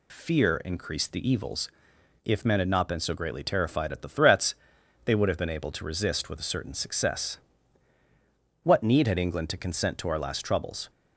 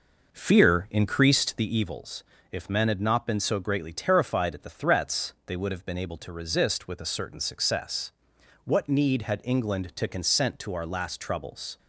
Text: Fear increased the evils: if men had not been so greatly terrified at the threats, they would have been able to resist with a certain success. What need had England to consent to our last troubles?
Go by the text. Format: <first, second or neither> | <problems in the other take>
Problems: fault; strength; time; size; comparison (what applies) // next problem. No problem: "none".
first | starts louder than the rest; noticeable; until 1.7 s; 5.5 dB